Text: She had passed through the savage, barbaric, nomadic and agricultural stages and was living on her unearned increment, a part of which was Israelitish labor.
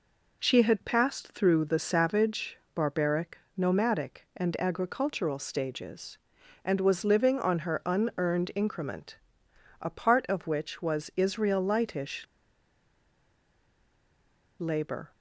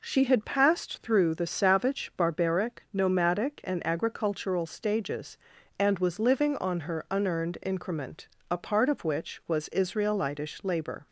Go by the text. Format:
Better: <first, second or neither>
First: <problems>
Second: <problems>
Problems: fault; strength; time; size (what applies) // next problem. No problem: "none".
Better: second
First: pauses between "Israelitish" and "labor"; strong; at 12.2 s; 2.3 s long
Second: none